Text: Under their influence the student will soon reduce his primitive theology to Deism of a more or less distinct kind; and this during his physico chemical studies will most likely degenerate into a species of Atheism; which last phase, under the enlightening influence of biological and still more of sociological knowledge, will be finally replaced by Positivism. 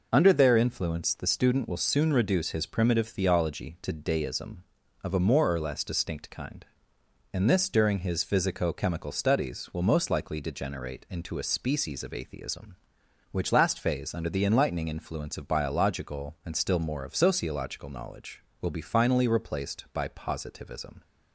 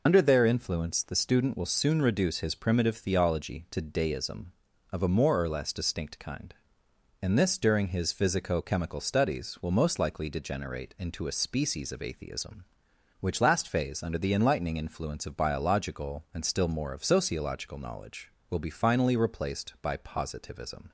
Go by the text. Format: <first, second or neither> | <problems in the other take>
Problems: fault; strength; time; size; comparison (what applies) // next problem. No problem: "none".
first | loses the start of "Under"; at 0.0 s; 45 ms